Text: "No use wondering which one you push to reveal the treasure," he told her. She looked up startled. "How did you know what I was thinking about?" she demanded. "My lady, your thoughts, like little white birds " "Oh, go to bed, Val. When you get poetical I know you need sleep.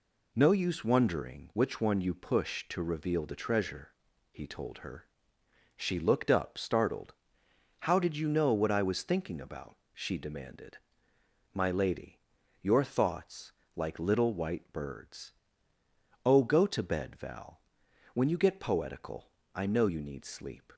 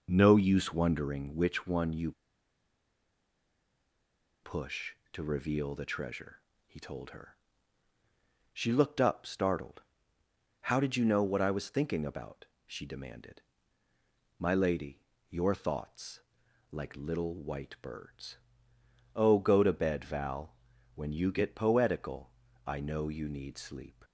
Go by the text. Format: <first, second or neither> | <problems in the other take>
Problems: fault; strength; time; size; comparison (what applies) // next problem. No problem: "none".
first | pauses between "you" and "push"; strong; at 2.1 s; 2.3 s long // pauses between "poetical" and "I"; slight; at 22.3 s; 0.34 s long; slight in the first